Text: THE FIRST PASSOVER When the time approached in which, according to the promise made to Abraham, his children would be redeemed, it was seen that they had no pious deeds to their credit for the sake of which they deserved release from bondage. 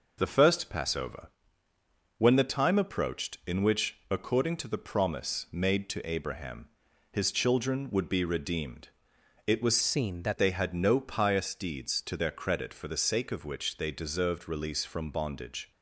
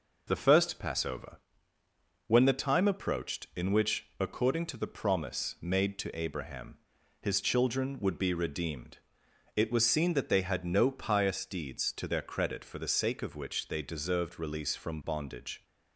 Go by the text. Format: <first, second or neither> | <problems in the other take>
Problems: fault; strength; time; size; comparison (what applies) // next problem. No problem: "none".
second | pauses between "PASSOVER" and "When"; noticeable; at 1.2 s; 0.88 s long; noticeable in the second // changes voice from "seen" to "that"; from 9.8 to 10.3 s; 0.5 s long